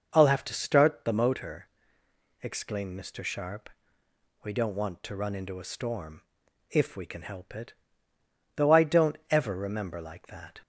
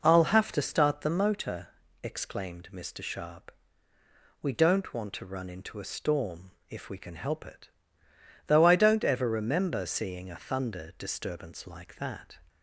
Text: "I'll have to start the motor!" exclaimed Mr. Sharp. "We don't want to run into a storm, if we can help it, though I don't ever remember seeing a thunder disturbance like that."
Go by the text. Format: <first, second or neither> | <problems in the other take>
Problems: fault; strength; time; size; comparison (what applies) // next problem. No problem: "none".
second | skips "seeing a thunder disturbance"; at 9.9 s